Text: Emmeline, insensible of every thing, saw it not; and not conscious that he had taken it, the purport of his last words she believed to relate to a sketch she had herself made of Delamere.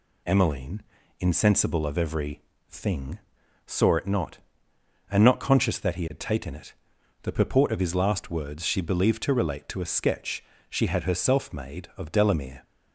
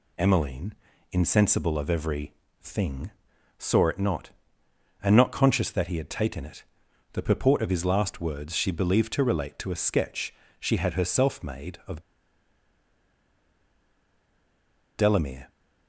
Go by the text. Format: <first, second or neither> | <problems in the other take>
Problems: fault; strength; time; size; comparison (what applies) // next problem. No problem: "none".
first | pauses between "every" and "thing"; slight; at 2.3 s; 0.30 s long; slight in the first // pauses between "sketch" and "she"; slight; at 10.3 s; 0.24 s long; slight in the first // pauses between "of" and "Delamere"; strong; at 12.0 s; 2.9 s long